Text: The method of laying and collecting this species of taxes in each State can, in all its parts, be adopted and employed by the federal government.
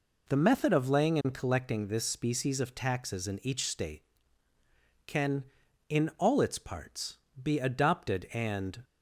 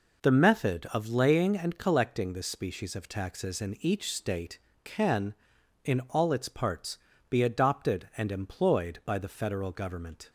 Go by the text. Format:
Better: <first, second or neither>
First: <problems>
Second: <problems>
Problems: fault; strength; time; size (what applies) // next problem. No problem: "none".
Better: second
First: stops before "employed by the federal government"; at 8.8 s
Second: none